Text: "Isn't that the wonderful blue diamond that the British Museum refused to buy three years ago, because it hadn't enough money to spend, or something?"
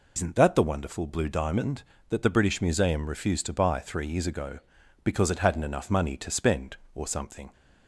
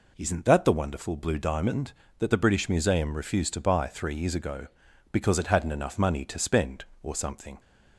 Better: second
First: loses the start of "Isn't"; at 0.1 s; 95 ms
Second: none

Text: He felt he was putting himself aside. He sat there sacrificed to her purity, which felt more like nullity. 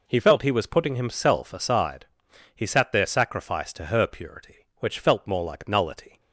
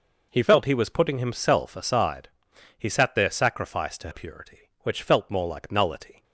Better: first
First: none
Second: skips "her"; at 4.1 s

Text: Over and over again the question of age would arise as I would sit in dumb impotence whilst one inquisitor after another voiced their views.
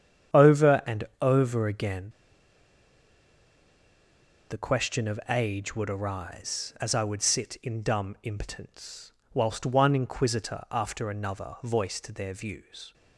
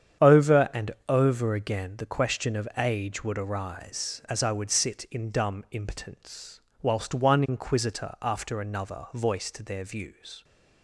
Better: second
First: starts louder than the rest; strong; until 1.5 s; 8.5 dB // pauses between "and" and "over"; slight; at 1.0 s; 0.18 s long // pauses between "again" and "the"; strong; at 2.0 s; 2.4 s long // pauses between "impotence" and "whilst"; slight; at 9.1 s; 0.20 s long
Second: starts louder than the rest; strong; until 1.4 s; 8.5 dB // pauses between "and" and "over"; slight; at 0.9 s; 0.18 s long // pauses between "impotence" and "whilst"; slight; at 6.6 s; 0.20 s long

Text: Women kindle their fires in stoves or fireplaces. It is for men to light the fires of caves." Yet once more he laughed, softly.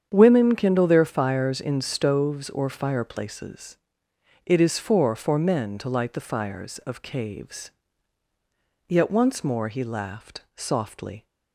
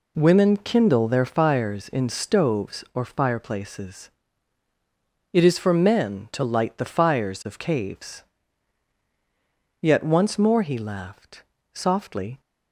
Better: second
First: starts louder than the rest; strong; until 1.1 s; 8 dB // says "for" twice; at 5.1 s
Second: none

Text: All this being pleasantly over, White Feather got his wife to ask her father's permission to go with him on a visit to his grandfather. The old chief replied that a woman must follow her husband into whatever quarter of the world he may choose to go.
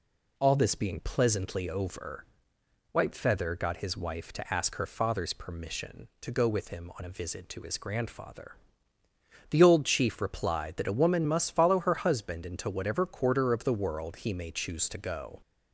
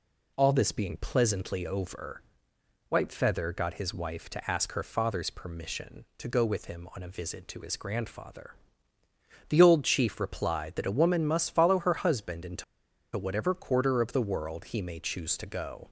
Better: first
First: none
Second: pauses between "into" and "whatever"; noticeable; at 12.6 s; 0.51 s long

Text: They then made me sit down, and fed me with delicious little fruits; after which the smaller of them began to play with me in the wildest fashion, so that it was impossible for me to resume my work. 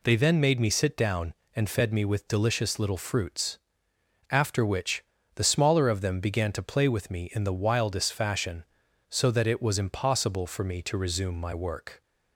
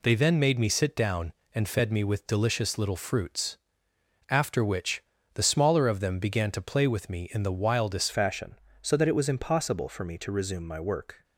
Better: first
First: pauses between "which" and "the"; slight; at 5.0 s; 0.32 s long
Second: pauses between "which" and "the"; slight; at 5.0 s; 0.32 s long // changes voice at "fashion"; from 8.1 s on; 3.1 s long

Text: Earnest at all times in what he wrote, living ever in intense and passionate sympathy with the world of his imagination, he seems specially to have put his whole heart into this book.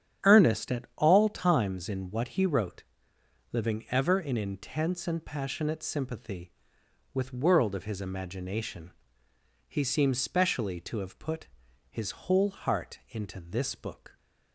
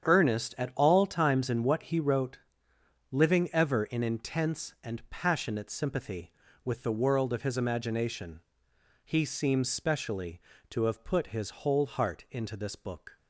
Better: second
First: starts louder than the rest; strong; until 1.3 s; 9 dB // skips "the"; at 7.3 s // pauses between "put" and "his"; at 11.4 s; 0.42 s long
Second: starts louder than the rest; strong; until 1.1 s; 8 dB

